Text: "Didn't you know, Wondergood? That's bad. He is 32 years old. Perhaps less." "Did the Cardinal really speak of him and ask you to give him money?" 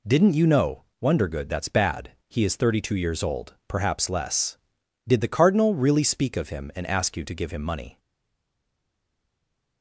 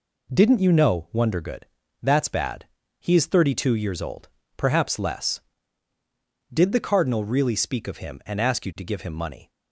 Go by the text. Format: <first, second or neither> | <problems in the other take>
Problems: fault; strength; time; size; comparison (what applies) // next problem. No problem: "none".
second | stays silent after the last word; noticeable; from 7.9 s on; 1.9 s long